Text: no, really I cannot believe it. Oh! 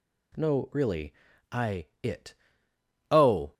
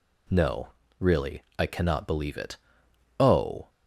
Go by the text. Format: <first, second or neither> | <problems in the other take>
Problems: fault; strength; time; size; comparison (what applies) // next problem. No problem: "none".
second | pauses between "really" and "I"; at 1.1 s; 0.38 s long; slight in the second // skips "cannot believe"; at 1.9 s